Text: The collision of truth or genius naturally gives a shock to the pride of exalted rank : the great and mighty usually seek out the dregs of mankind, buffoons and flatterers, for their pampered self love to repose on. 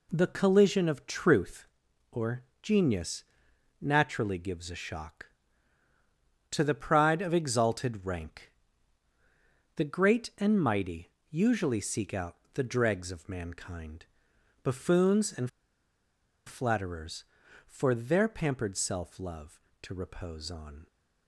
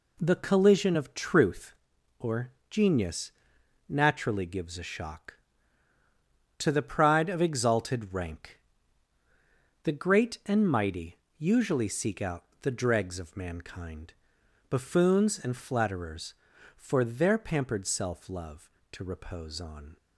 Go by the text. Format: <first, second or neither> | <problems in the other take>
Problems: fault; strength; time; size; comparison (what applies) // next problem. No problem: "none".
second | pauses between "or" and "genius"; slight; at 2.4 s; 0.20 s long; slight in the second // pauses between "genius" and "naturally"; noticeable; at 3.2 s; 0.58 s long; noticeable in the second // pauses between "mighty" and "usually"; slight; at 11.1 s; 0.20 s long; slight in the second // pauses between "out" and "the"; slight; at 12.3 s; 0.20 s long; slight in the second // pauses between "and" and "flatterers"; at 15.4 s; 0.98 s long